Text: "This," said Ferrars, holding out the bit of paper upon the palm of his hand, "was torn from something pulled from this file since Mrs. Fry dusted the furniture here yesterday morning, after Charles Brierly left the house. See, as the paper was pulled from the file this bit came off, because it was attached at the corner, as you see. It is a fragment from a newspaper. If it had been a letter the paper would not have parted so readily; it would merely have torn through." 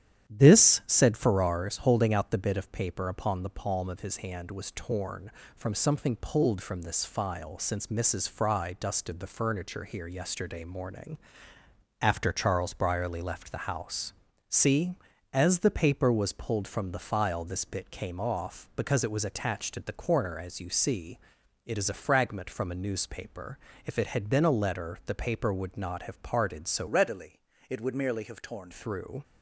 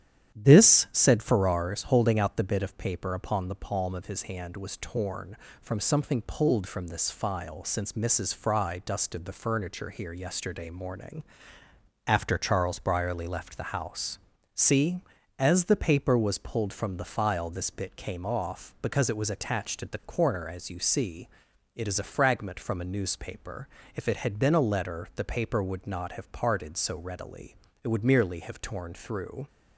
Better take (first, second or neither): second